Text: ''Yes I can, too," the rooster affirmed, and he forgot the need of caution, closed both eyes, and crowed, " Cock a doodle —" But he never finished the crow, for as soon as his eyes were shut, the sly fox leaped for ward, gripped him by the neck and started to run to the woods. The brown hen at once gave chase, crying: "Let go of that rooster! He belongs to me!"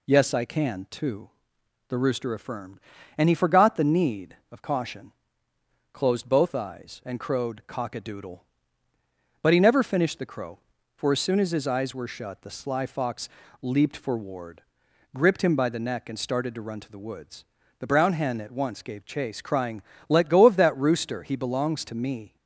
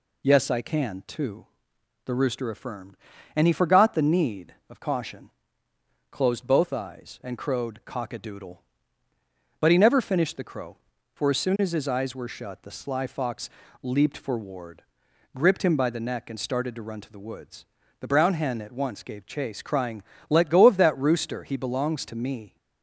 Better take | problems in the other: neither | pauses between "fox" and "leaped"; slight; the same in both

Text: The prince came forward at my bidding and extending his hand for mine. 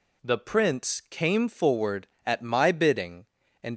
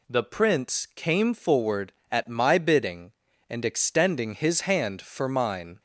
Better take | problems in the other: second | stops before "extending his hand for mine"; at 3.7 s

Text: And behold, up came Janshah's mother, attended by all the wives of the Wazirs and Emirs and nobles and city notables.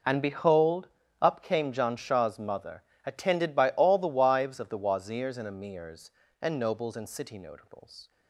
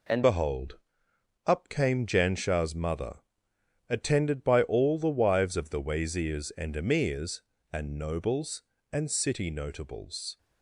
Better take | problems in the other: first | changes voice at "behold"; from 0.2 s on; 10.1 s long

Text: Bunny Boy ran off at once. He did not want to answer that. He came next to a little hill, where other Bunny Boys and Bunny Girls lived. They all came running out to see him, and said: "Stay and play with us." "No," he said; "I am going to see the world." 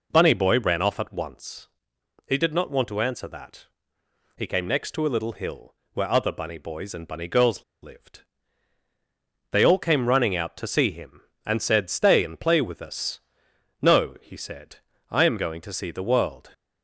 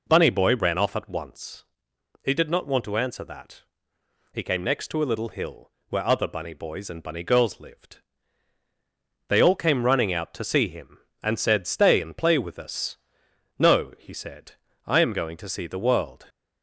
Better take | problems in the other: second | pauses between "Girls" and "lived"; slight; at 7.6 s; 0.19 s long

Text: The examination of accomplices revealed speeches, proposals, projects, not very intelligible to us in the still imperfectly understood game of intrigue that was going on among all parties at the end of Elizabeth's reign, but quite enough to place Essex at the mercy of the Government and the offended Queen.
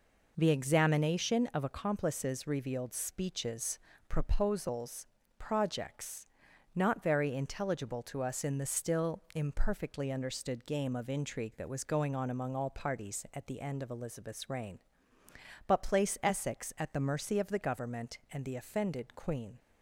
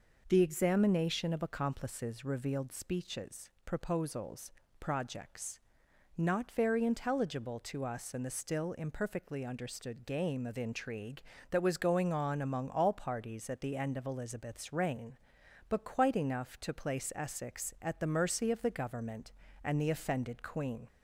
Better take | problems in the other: second | skips "quite enough to"; at 15.8 s

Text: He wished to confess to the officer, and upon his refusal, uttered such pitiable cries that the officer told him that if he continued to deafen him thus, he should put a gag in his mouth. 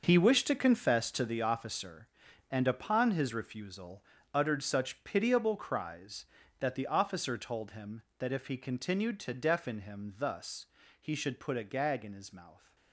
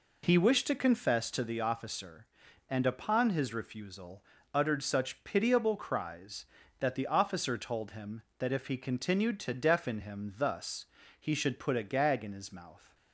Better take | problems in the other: second | gets quieter; strong; throughout; 12 dB

